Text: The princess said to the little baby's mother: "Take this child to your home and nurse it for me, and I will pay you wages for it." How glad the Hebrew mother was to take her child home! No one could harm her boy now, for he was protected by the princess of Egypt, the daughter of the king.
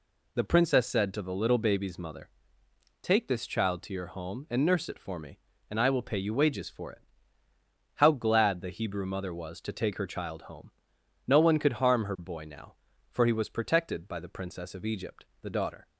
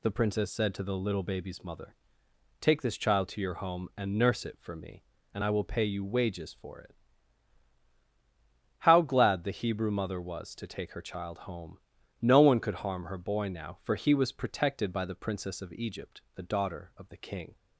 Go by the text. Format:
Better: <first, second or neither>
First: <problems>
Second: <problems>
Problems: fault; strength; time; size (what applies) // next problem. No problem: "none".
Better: second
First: stops before "of the king"; at 15.8 s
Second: none